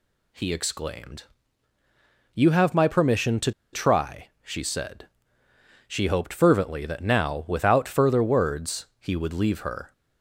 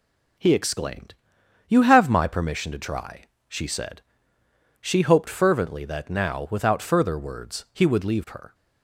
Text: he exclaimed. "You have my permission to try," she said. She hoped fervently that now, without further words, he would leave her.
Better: second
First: pauses between "to" and "try"; slight; at 3.5 s; 0.22 s long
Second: none

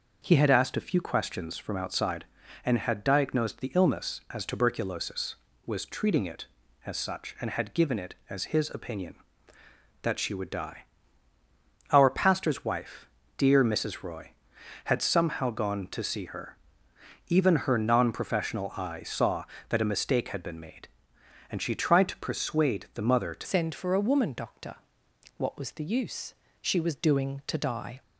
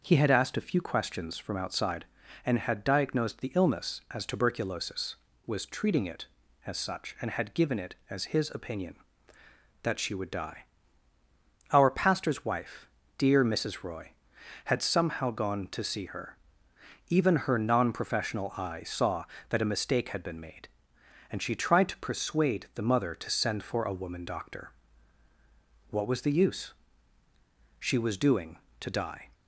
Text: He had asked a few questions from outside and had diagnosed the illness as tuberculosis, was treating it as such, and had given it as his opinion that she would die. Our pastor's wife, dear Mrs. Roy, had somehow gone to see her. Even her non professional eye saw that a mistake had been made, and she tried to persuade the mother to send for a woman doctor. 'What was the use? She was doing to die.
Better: second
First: changes voice at "send"; from 23.4 s on; 4.6 s long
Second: none

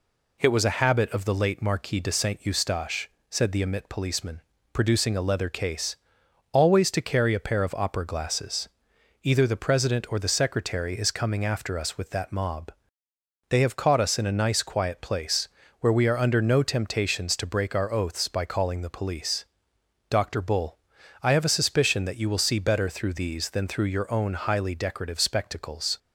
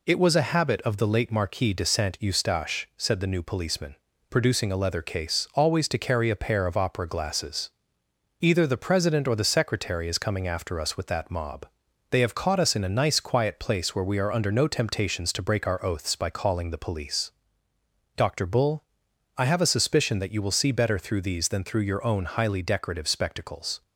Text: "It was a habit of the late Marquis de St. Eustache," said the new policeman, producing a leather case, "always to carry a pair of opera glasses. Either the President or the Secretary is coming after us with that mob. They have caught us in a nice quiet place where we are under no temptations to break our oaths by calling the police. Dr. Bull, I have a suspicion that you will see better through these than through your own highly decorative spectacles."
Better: second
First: says "emit" for "new"; at 3.6 s // pauses between "place" and "where"; slight; at 15.4 s; 0.32 s long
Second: none

